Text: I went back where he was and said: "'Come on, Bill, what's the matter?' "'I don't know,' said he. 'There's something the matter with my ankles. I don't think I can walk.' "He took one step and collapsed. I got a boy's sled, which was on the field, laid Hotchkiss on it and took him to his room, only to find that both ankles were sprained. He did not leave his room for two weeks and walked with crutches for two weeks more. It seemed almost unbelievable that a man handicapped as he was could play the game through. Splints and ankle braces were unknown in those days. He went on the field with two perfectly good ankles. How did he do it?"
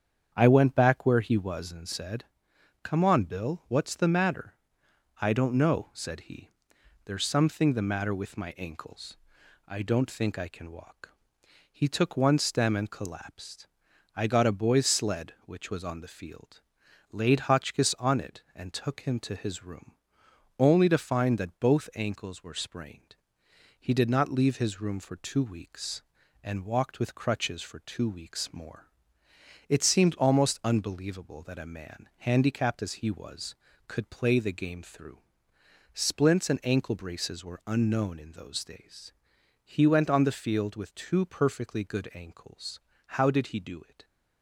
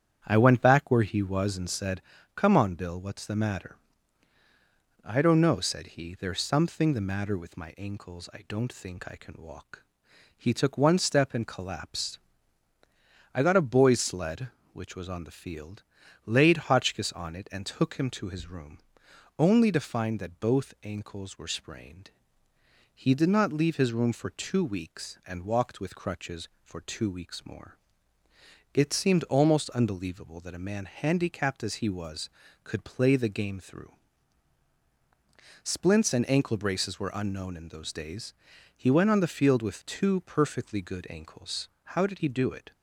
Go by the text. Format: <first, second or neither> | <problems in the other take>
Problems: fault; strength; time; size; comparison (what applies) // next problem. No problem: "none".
second | starts louder than the rest; strong; until 1.3 s; 8 dB; strong in the second // says "stem" for "step"; at 12.3 s